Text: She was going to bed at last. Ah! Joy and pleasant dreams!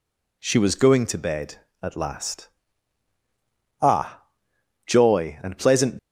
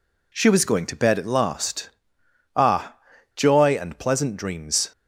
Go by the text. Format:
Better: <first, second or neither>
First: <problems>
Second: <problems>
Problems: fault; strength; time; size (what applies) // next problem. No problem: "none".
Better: second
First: stops before "dreams"; at 5.9 s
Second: none